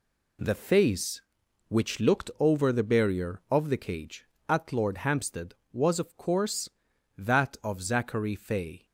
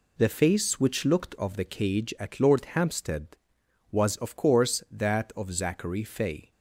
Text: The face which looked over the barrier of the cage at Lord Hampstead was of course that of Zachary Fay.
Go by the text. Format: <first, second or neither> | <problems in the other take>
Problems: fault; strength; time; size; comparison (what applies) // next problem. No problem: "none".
first | skips "over the barrier"; at 1.3 s